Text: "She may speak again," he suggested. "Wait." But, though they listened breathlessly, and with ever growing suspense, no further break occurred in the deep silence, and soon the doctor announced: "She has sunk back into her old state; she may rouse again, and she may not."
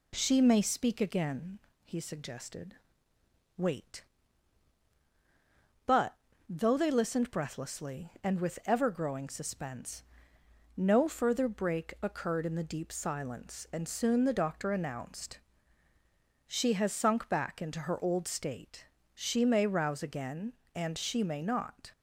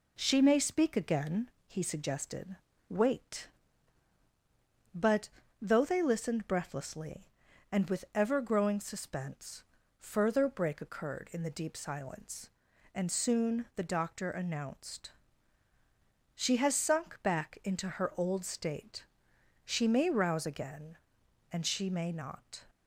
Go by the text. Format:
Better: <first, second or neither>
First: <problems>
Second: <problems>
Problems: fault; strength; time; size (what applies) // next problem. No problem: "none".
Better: first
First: none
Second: skips "no"; at 9.8 s